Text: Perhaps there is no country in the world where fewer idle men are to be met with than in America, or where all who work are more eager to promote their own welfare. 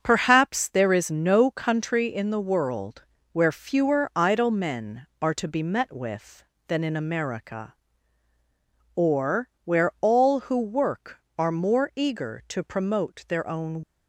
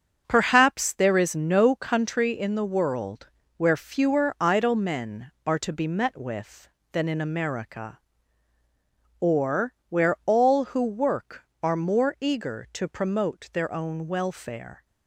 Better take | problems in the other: second | starts louder than the rest; until 1.0 s; 6.5 dB; also in the second // pauses between "world" and "where"; slight; at 3.0 s; 0.30 s long; slight in the second // pauses between "or" and "where"; slight; at 9.5 s; 0.16 s long; slight in the second // stops before "welfare"; at 13.8 s

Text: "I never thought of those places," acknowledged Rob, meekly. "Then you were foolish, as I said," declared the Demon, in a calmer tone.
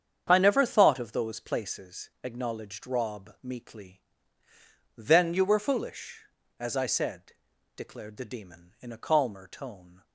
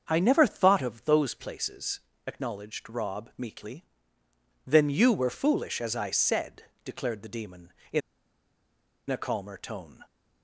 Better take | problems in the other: first | starts louder than the rest; until 1.0 s; 7 dB; strong in the first // pauses between "in" and "a"; at 8.0 s; 1.0 s long

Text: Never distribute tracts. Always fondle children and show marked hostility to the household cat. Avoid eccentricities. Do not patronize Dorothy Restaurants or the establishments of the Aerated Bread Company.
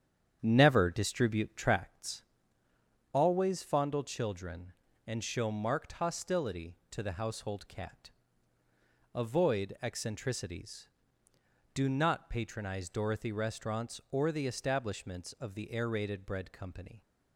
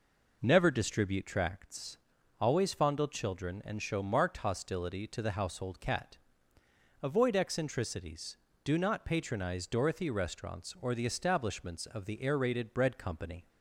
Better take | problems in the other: second | starts louder than the rest; strong; until 2.0 s; 9 dB

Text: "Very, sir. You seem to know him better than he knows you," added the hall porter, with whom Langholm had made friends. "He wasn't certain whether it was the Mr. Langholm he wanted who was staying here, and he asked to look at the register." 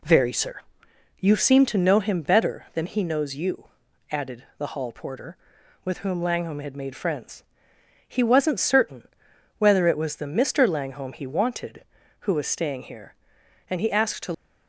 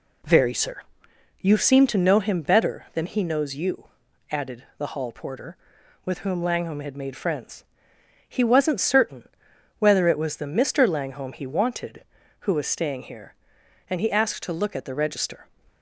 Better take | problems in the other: second | pauses between "certain" and "whether"; noticeable; at 9.0 s; 0.50 s long; noticeable in the second // stops before "look at the register"; at 14.3 s

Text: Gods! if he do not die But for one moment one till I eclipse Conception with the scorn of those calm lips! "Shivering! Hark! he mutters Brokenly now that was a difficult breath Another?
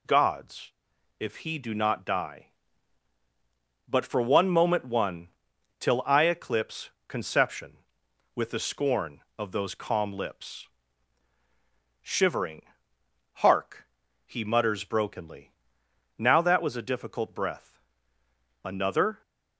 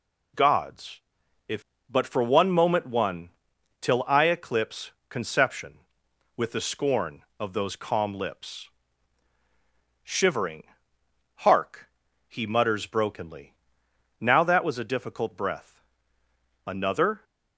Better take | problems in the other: first | skips "he do not die"; at 1.7 s // pauses between "one" and "till"; noticeable; at 3.2 s; 0.52 s long; noticeable in the first // pauses between "eclipse" and "Conception"; slight; at 4.9 s; 0.18 s long; slight in the first // pauses between "Brokenly" and "now"; noticeable; at 13.5 s; 0.66 s long; noticeable in the first // pauses between "breath" and "Another"; noticeable; at 15.8 s; 0.84 s long; noticeable in the first

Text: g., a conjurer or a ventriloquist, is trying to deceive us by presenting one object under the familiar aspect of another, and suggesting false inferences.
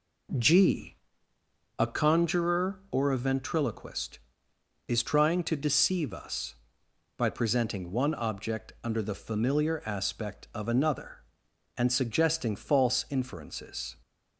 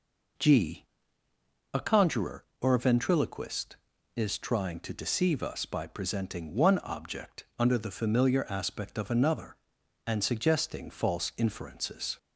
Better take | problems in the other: neither | none

